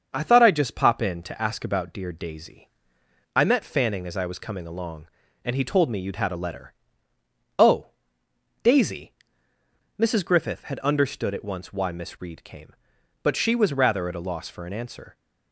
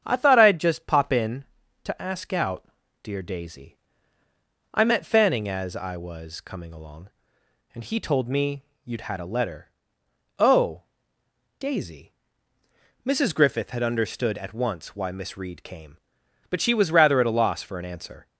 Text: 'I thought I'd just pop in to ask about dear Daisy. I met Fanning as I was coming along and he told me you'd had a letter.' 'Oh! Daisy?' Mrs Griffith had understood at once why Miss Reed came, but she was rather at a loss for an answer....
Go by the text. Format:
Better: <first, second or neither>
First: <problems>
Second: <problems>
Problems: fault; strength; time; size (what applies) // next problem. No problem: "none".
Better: first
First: starts louder than the rest; until 1.1 s; 6.5 dB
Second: starts louder than the rest; strong; until 1.0 s; 8.5 dB // says "out" for "about"; at 2.3 s // pauses between "me" and "you'd"; slight; at 8.6 s; 0.20 s long